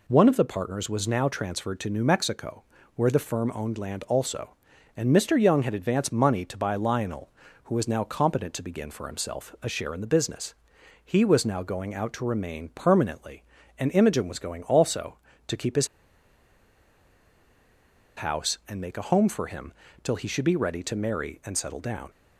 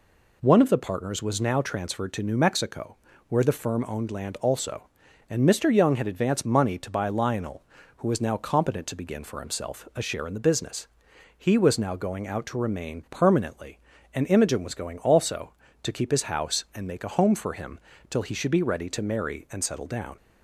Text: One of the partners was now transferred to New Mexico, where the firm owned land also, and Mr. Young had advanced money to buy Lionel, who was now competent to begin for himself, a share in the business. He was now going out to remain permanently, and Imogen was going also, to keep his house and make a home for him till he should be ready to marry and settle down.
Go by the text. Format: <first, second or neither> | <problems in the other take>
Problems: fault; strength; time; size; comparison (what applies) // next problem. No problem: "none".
second | pauses between "his" and "house"; strong; at 15.8 s; 2.2 s long // pauses between "him" and "till"; slight; at 19.7 s; 0.32 s long; slight in the second